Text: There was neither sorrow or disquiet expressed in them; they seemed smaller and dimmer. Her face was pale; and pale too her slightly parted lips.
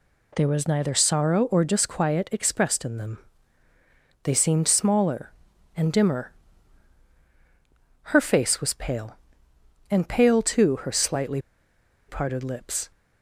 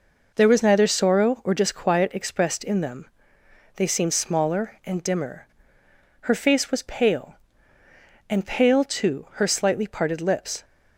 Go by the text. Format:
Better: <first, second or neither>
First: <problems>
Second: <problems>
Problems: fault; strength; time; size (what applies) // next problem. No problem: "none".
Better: second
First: pauses between "slightly" and "parted"; noticeable; at 11.3 s; 0.68 s long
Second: none